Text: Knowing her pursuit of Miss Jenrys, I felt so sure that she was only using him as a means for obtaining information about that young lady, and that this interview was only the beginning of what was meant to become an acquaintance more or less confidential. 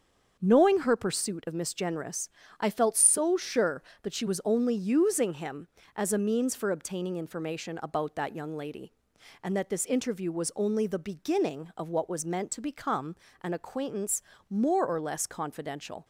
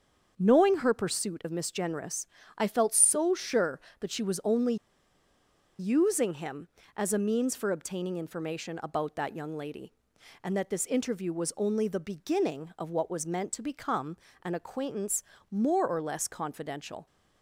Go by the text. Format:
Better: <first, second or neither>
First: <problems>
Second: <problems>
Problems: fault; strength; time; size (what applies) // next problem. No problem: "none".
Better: first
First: starts louder than the rest; until 1.4 s; 7 dB // pauses between "become" and "an"; slight; at 13.1 s; 0.28 s long // pauses between "acquaintance" and "more"; slight; at 14.2 s; 0.28 s long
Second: starts louder than the rest; until 1.3 s; 7 dB // pauses between "only" and "using"; at 4.7 s; 1.0 s long // pauses between "become" and "an"; slight; at 14.1 s; 0.28 s long // pauses between "acquaintance" and "more"; slight; at 15.2 s; 0.28 s long